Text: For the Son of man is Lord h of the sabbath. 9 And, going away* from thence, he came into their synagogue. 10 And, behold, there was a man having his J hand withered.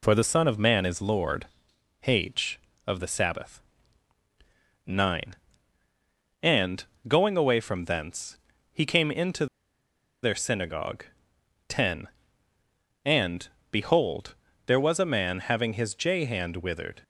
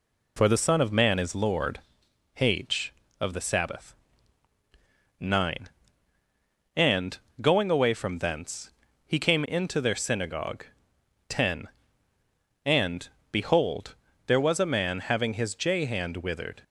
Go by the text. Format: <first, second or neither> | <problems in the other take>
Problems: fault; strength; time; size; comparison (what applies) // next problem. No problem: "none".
second | pauses between "Lord" and "h"; noticeable; at 1.4 s; 0.58 s long; noticeable in the second // pauses between "into" and "their"; noticeable; at 9.4 s; 0.77 s long